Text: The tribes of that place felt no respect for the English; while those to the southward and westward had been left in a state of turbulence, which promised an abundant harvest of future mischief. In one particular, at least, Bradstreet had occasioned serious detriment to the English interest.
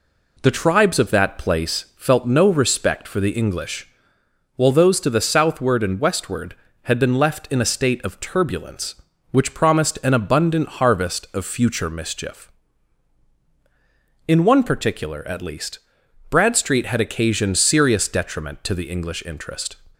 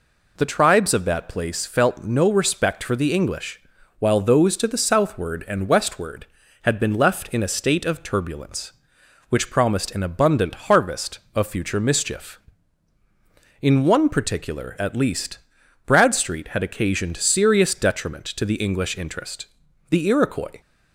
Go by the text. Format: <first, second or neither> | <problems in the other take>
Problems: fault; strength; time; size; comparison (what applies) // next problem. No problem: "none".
first | goes on to say "The Iroquois"; noticeable; from 19.8 s on; 0.72 s long